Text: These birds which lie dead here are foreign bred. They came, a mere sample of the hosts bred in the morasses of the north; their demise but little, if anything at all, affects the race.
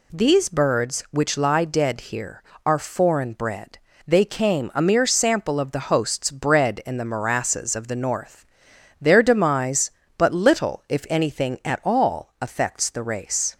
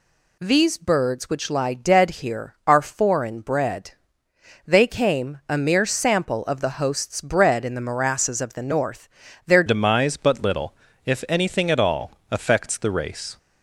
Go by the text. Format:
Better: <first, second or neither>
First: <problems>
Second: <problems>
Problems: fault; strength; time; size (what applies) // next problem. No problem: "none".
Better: first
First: none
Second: changes voice at "demise"; from 9.6 s on; 3.7 s long